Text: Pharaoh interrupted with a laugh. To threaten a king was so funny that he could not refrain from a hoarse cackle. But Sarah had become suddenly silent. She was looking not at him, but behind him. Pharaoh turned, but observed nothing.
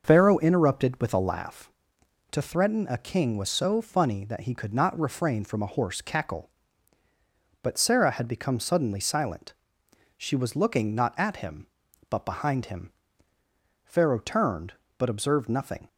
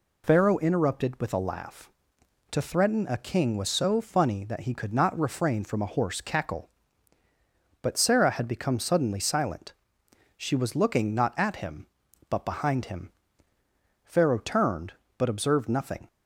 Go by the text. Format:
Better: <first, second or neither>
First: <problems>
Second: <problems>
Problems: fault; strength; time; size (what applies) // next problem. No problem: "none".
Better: second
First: starts louder than the rest; until 1.6 s; 6 dB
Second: none